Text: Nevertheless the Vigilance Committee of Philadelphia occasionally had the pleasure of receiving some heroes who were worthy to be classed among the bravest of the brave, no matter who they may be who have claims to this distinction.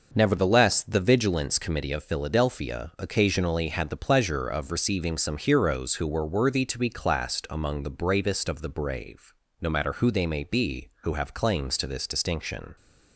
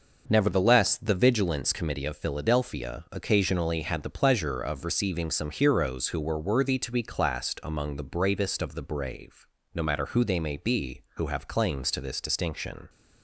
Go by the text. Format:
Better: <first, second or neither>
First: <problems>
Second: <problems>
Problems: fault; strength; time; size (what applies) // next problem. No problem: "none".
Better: neither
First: none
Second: none